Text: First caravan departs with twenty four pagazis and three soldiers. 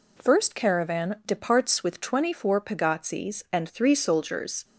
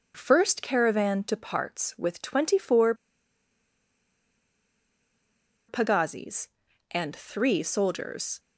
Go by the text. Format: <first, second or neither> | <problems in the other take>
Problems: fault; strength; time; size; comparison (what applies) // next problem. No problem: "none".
first | starts louder than the rest; until 1.1 s; 6 dB // pauses between "four" and "pagazis"; strong; at 2.9 s; 2.7 s long